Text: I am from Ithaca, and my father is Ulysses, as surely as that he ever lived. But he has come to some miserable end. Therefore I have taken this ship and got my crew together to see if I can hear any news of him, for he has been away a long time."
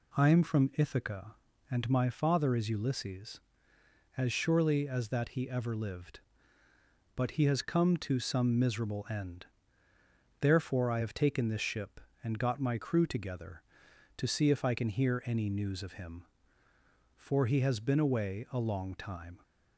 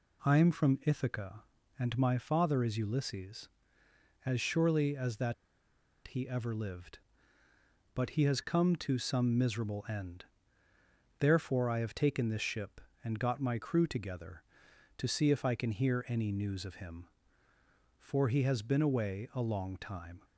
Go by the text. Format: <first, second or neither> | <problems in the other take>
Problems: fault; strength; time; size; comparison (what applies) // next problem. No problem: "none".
first | pauses between "that" and "he"; noticeable; at 5.3 s; 0.72 s long